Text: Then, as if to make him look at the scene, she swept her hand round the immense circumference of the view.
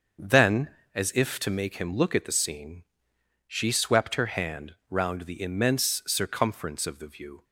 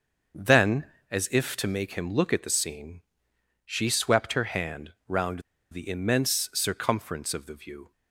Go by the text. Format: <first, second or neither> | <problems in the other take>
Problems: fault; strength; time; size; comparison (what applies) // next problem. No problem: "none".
first | starts louder than the rest; until 1.6 s; 6.5 dB; also in the first // pauses between "hand" and "round"; slight; at 4.9 s; 0.16 s long; slight in the first // pauses between "round" and "the"; slight; at 5.3 s; 0.31 s long